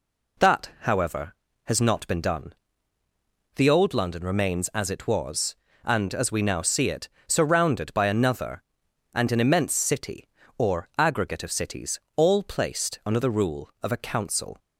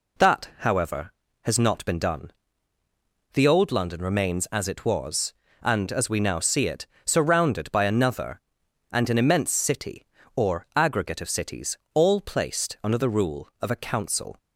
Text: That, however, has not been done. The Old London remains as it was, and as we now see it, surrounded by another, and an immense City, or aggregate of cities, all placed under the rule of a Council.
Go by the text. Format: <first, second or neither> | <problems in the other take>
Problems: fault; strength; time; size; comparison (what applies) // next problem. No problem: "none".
neither | none